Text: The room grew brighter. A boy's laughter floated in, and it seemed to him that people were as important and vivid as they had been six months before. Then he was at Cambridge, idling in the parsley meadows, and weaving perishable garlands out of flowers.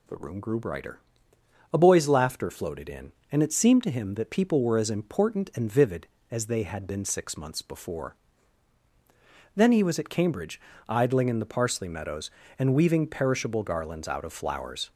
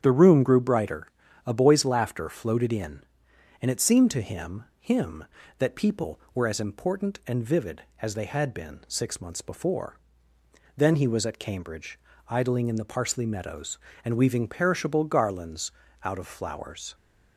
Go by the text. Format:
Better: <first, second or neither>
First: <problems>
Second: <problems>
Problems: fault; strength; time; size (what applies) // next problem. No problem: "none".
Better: first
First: none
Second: starts louder than the rest; strong; until 1.0 s; 8.5 dB // says "him" twice; at 4.7 s // pauses between "garlands" and "out"; slight; at 15.7 s; 0.32 s long